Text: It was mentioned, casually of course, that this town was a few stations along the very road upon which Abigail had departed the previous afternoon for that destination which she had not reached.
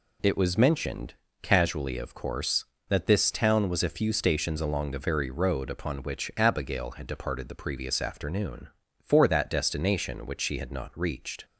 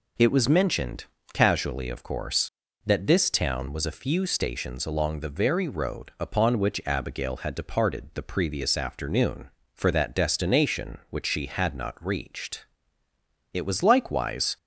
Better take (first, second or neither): first